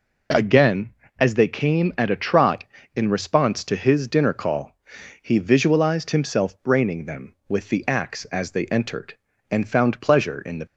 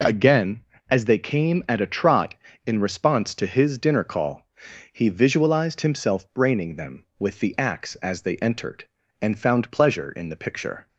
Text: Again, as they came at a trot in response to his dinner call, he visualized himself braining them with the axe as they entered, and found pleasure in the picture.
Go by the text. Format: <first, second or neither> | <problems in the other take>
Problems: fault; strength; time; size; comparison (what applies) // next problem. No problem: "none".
second | stops before "picture"; at 10.6 s